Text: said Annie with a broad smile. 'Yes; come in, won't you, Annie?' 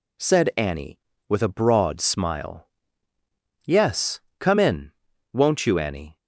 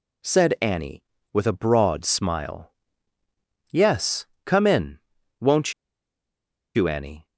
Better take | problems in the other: first | pauses between "won't" and "you"; at 5.7 s; 1.0 s long

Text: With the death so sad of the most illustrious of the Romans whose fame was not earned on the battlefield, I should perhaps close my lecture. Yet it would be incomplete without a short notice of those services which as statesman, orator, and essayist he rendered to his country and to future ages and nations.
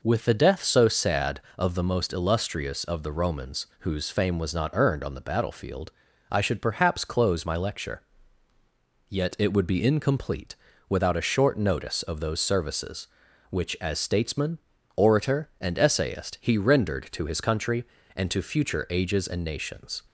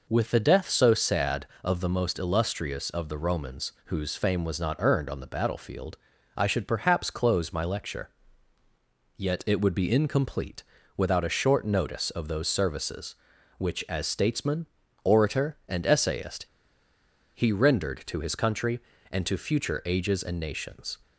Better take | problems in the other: first | pauses between "incomplete" and "without"; slight; at 10.6 s; 0.34 s long; slight in the first // pauses between "essayist" and "he"; noticeable; at 16.4 s; 0.88 s long

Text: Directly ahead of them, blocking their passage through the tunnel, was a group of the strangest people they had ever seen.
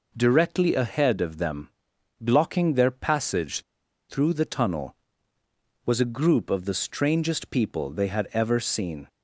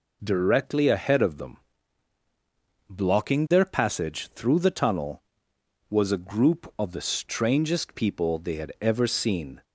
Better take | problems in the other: second | pauses between "passage" and "through"; noticeable; at 3.6 s; 0.46 s long

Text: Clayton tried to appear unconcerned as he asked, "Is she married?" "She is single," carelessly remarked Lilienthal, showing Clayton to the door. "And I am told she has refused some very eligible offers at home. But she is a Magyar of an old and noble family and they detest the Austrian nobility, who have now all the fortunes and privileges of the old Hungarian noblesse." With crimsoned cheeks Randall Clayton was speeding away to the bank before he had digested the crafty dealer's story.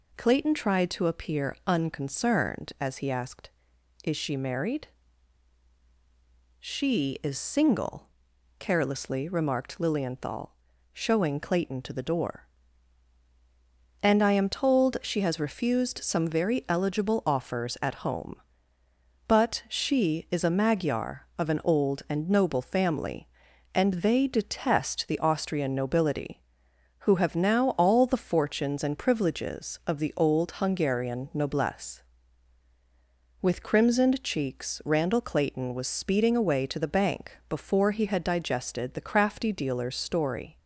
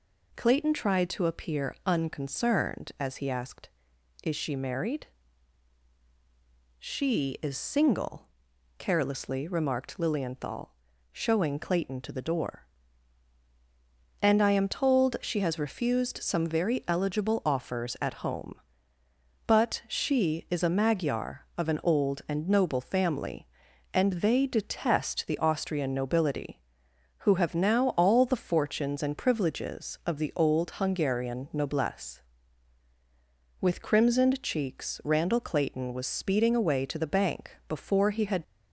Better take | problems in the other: first | stops before "digested the crafty dealer's story"; at 38.4 s

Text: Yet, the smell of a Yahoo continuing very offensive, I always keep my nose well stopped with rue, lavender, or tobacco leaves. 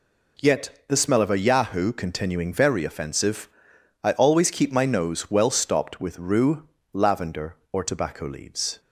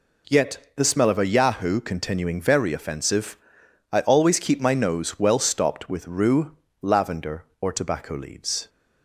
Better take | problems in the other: neither | none

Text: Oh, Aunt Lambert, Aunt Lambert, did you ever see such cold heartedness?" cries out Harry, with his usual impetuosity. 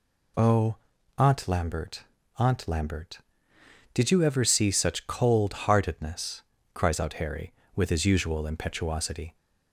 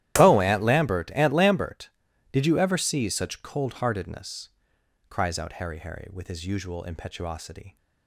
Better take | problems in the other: first | starts louder than the rest; strong; until 1.2 s; 13.5 dB // says "Harry" twice; at 5.7 s

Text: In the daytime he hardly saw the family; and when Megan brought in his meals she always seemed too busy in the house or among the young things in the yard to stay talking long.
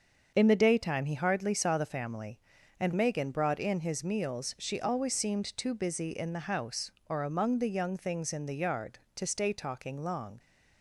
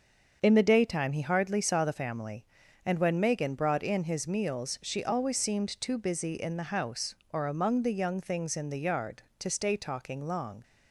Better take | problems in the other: second | starts louder than the rest; until 1.3 s; 7 dB; also in the second // skips "when"; at 2.9 s

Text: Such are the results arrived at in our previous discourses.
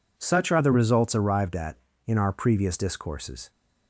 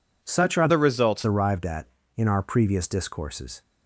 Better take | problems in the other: first | changes voice from "the" to "results"; from 0.6 to 1.2 s; 0.6 s long

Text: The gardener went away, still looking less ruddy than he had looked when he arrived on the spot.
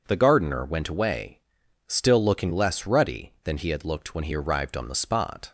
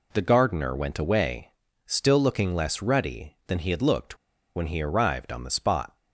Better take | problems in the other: first | pauses between "looked" and "when"; at 4.1 s; 0.38 s long

